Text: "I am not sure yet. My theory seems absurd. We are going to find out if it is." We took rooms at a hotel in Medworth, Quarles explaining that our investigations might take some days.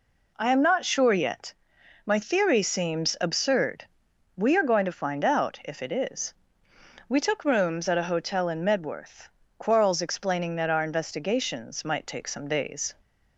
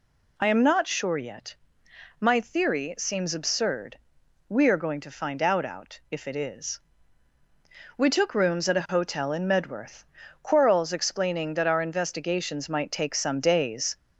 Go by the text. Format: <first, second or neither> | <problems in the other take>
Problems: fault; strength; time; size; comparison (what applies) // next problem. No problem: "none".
first | says "out" twice; at 5.6 s